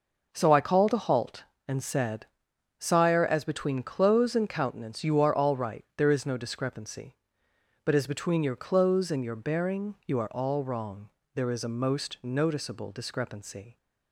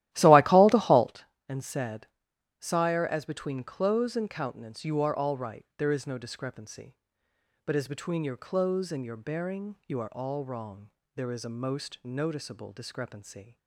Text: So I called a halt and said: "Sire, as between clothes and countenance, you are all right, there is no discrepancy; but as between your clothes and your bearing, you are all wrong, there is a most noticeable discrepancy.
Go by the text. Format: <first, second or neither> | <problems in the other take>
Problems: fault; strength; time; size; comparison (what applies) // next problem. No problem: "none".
first | starts louder than the rest; strong; until 1.1 s; 14.5 dB